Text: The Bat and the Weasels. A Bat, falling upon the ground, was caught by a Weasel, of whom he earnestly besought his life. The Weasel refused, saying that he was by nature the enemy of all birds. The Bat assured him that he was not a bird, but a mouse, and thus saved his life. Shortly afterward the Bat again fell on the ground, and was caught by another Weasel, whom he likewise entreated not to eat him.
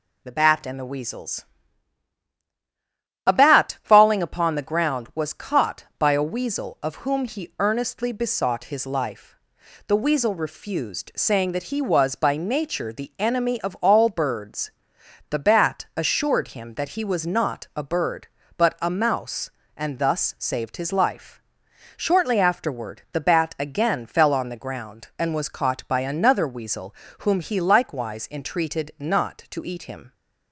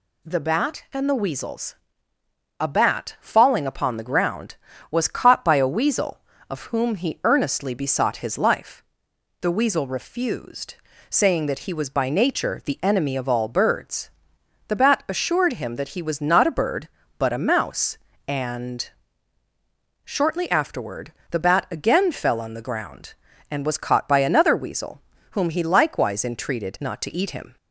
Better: first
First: none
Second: skips "thus saved his life"; at 19.4 s // pauses between "afterward" and "the"; slight; at 21.1 s; 0.20 s long

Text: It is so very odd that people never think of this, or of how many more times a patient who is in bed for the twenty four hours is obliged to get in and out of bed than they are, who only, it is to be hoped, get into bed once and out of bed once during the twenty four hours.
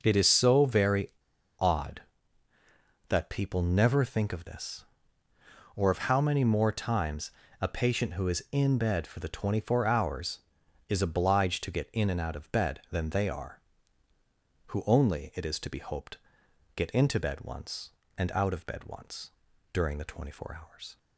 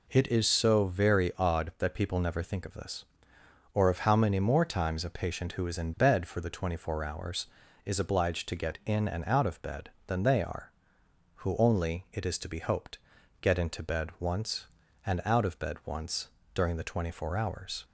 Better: second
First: pauses between "very" and "odd"; noticeable; at 1.0 s; 0.51 s long // pauses between "times" and "a"; slight; at 7.3 s; 0.28 s long // pauses between "once" and "during"; at 19.3 s; 0.42 s long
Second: pauses between "once" and "during"; slight; at 16.2 s; 0.26 s long

